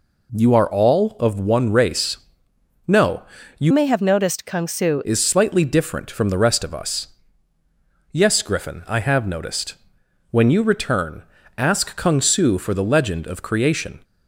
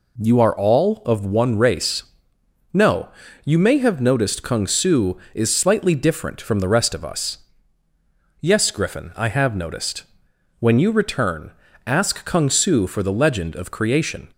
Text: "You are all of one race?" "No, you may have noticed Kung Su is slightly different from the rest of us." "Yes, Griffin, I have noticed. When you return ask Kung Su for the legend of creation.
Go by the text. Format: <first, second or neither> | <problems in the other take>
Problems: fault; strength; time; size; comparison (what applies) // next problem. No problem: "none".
second | changes voice from "may" to "Su"; from 3.7 to 5.0 s; 1.3 s long // pauses between "return" and "ask"; slight; at 11.2 s; 0.36 s long; slight in the second